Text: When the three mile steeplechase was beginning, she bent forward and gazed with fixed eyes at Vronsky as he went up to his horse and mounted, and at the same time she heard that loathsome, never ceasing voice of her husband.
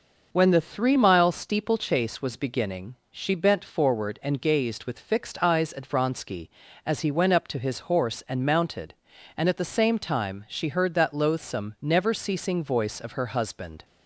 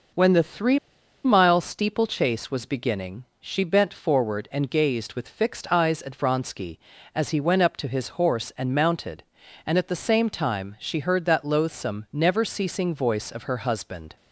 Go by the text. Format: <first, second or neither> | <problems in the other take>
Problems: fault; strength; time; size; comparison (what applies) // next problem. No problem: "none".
first | pauses between "three" and "mile"; noticeable; at 0.7 s; 0.46 s long